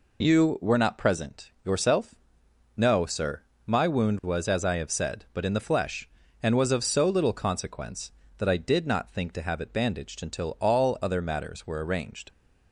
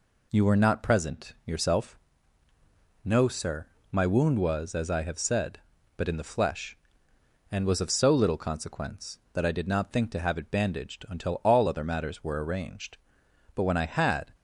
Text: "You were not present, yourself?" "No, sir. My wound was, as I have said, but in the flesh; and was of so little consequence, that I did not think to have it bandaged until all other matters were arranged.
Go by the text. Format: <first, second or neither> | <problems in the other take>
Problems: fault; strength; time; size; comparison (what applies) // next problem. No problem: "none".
first | goes on to say "But when I had"; noticeable; from 13.5 s on; 0.80 s long